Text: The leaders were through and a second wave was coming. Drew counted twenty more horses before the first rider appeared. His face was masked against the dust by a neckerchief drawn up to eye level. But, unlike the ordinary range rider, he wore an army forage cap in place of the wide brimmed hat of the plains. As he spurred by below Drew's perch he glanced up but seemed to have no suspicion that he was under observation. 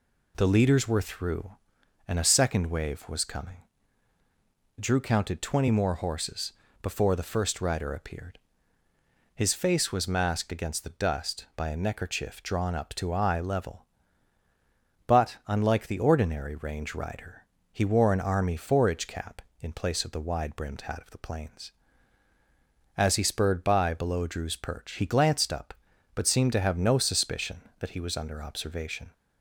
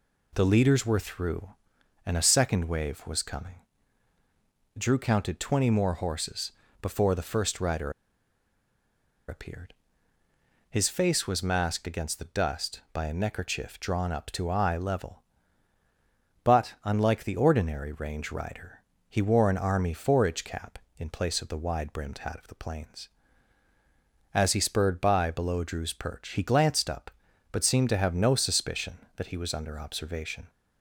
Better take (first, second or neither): first